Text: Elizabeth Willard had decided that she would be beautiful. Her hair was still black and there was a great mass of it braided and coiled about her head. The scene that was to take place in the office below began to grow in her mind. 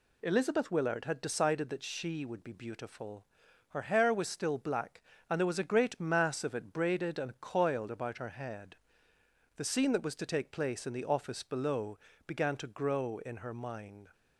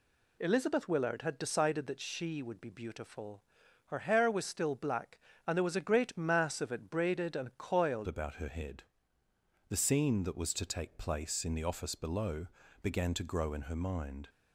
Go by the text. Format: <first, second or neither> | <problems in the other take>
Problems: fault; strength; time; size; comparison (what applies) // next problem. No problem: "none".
first | changes voice at "about"; from 8.0 s on; 6.2 s long // pauses between "below" and "began"; slight; at 12.4 s; 0.34 s long; slight in the first